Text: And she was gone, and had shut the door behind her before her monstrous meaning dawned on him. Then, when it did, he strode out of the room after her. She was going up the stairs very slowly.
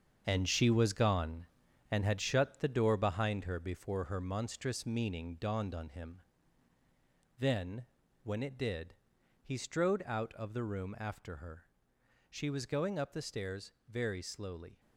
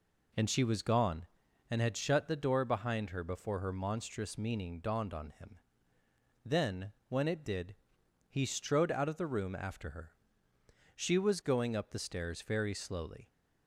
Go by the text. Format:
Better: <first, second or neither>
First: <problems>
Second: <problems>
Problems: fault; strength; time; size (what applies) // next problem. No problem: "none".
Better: second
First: gets quieter; strong; throughout; 8.5 dB // pauses between "stairs" and "very"; slight; at 13.7 s; 0.16 s long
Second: none